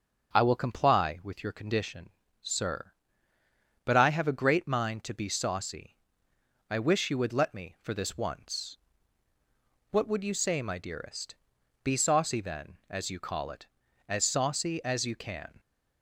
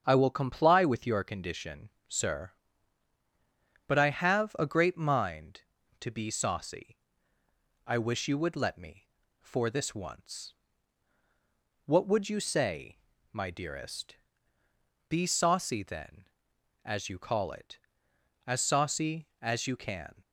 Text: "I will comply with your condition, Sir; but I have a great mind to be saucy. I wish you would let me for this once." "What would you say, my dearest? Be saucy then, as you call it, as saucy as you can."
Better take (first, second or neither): neither